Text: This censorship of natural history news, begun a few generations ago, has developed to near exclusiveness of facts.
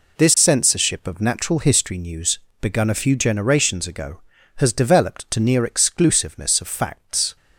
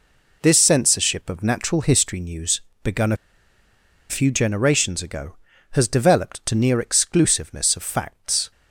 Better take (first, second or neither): first